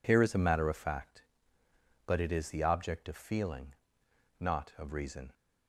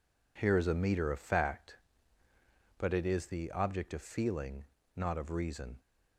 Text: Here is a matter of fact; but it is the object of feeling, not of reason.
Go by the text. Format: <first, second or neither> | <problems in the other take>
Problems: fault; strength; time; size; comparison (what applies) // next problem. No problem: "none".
first | says "meter" for "matter"; at 0.7 s